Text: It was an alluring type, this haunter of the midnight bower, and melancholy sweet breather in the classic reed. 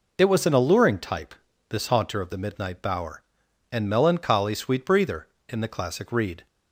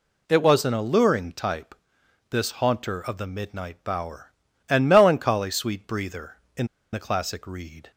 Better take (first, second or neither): first